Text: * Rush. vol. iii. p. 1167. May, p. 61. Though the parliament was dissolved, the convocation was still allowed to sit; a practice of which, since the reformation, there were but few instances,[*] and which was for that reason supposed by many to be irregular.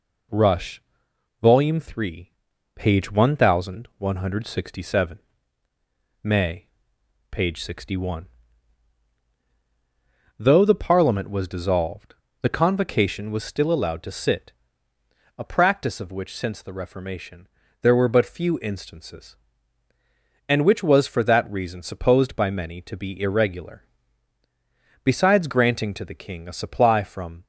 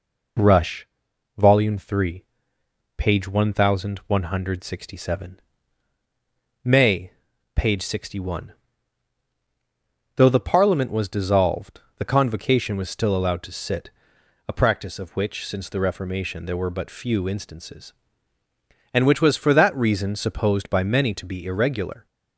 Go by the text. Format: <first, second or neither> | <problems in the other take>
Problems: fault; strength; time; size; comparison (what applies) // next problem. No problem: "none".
second | goes on to say "Besides granting to the king a supply from"; strong; from 25.0 s on; 2.4 s long